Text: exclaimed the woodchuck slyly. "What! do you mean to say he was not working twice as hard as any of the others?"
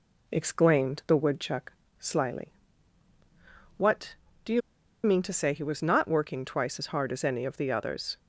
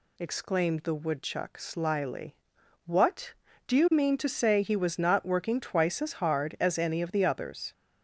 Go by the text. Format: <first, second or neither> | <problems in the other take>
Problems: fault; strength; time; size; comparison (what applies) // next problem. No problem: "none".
second | pauses between "woodchuck" and "slyly"; slight; at 1.7 s; 0.30 s long // pauses between "you" and "mean"; at 4.6 s; 0.43 s long